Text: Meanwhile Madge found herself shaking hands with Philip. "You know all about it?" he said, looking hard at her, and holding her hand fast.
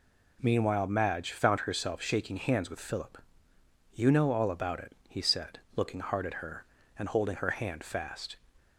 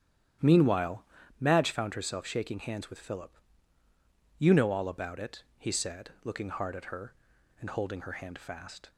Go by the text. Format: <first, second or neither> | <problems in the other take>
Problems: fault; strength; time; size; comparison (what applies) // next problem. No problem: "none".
first | starts louder than the rest; strong; until 1.3 s; 11 dB // pauses between "Meanwhile" and "Madge"; slight; at 1.0 s; 0.36 s long